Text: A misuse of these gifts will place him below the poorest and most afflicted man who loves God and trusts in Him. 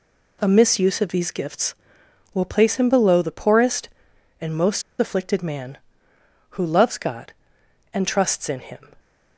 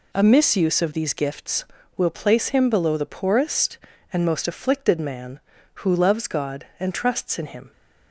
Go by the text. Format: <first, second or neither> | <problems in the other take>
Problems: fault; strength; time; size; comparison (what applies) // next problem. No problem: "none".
second | pauses between "most" and "afflicted"; slight; at 4.8 s; 0.17 s long